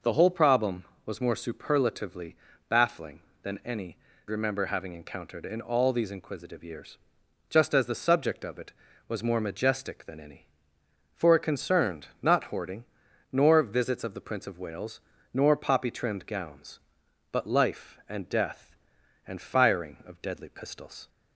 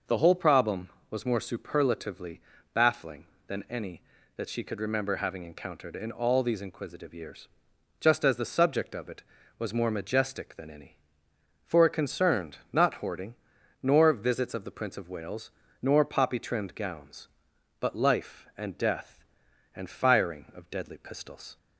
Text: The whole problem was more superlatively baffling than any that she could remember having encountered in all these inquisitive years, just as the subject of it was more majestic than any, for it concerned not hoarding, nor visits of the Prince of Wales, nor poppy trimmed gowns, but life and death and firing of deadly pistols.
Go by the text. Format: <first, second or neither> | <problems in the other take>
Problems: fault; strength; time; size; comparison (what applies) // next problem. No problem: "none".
second | pauses between "superlatively" and "baffling"; slight; at 2.3 s; 0.34 s long; slight in the second // skips "that she could"; at 4.1 s